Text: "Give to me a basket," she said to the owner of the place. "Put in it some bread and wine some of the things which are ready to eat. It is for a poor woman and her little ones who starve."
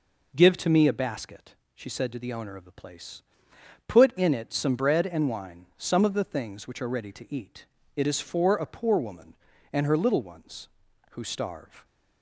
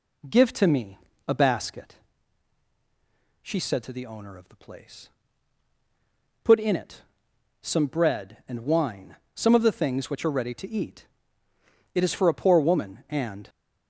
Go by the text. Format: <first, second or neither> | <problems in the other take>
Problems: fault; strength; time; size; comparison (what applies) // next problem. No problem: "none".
first | pauses between "me" and "a"; slight; at 0.9 s; 0.30 s long // pauses between "it" and "some"; noticeable; at 7.0 s; 0.58 s long // pauses between "wine" and "some"; slight; at 9.1 s; 0.20 s long // stops before "her little ones who starve"; at 13.4 s